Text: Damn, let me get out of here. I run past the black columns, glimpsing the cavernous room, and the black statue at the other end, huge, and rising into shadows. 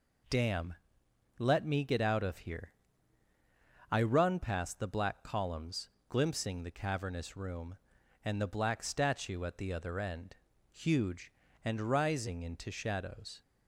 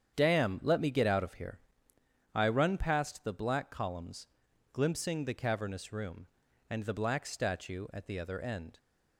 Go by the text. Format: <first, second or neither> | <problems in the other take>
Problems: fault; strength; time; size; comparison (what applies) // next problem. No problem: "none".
first | starts louder than the rest; strong; until 1.1 s; 8.5 dB // stops before "huge and rising into shadows"; at 8.7 s